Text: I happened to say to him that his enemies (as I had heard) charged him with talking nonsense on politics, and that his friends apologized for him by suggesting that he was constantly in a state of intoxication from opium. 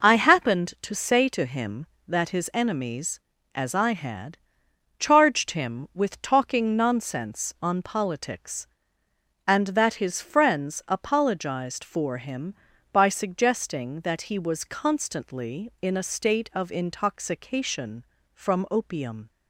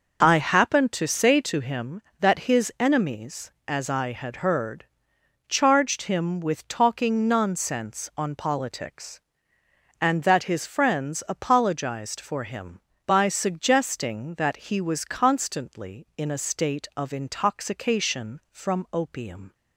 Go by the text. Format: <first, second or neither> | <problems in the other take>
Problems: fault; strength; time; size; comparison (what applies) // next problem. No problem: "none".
second | skips "heard"; at 4.6 s